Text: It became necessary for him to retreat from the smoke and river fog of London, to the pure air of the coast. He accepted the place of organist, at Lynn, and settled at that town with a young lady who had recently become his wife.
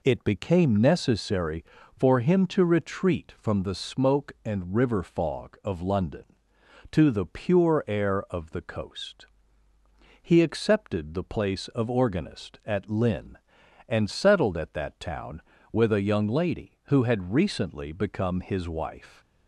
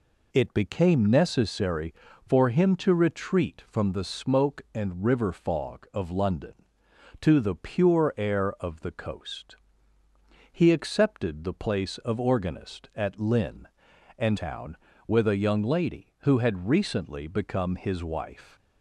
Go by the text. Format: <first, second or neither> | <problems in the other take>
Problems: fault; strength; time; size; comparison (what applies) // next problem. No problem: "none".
first | skips "settled at that"; at 14.3 s